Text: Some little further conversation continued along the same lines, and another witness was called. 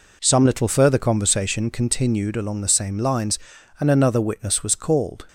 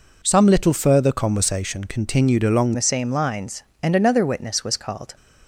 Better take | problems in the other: first | changes voice at "the"; from 2.7 s on; 2.4 s long

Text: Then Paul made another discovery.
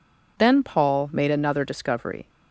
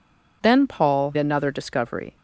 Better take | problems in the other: first | skips "made"; at 1.1 s

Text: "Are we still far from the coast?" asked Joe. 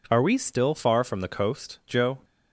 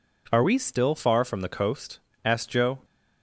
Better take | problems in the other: second | skips "asked"; at 1.8 s

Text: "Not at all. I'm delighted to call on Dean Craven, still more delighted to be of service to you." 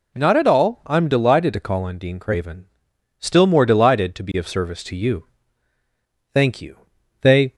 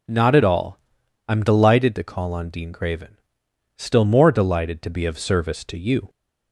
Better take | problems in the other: second | goes on to say "Thank you They"; noticeable; from 6.3 s on; 1.2 s long

